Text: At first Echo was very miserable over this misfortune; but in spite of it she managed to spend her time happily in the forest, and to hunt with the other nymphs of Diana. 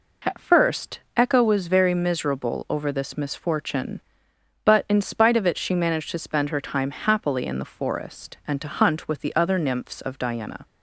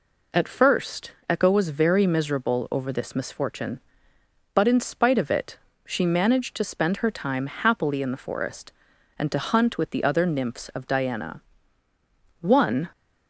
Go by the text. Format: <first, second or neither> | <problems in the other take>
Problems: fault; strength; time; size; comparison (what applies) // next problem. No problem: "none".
first | pauses between "first" and "Echo"; slight; at 1.1 s; 0.16 s long; slight in the first // pauses between "it" and "she"; slight; at 5.5 s; 0.28 s long // goes on to say "One"; slight; from 12.4 s on; 0.48 s long